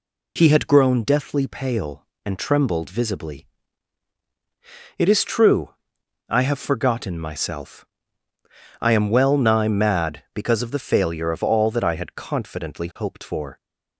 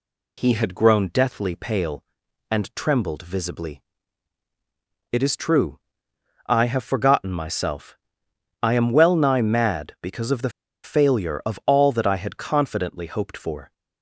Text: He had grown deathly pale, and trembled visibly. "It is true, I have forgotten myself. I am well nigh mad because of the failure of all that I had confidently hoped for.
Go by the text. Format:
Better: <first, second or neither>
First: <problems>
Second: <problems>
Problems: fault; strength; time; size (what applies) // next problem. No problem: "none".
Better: first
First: none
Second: pauses between "the" and "failure"; slight; at 10.5 s; 0.35 s long